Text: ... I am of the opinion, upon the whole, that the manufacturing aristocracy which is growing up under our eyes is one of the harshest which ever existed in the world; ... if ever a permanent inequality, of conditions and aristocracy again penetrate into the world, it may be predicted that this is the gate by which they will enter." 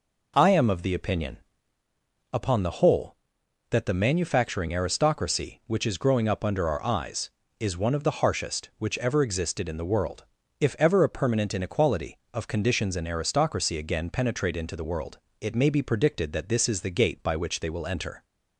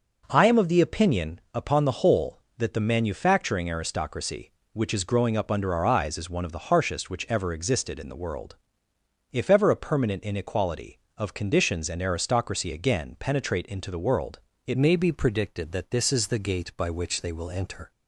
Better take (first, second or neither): first